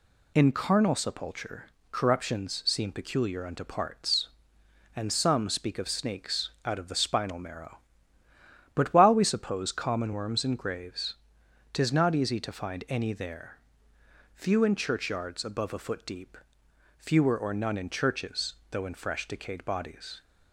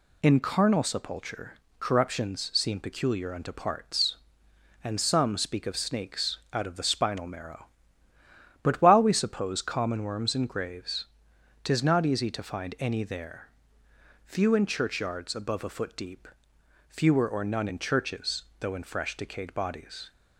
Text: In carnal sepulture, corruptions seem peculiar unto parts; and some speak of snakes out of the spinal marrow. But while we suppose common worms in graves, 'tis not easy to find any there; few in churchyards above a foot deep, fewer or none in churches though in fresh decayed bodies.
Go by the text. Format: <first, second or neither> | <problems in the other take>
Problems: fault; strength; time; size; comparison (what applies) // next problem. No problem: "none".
neither | pauses between "churches" and "though"; slight; the same in both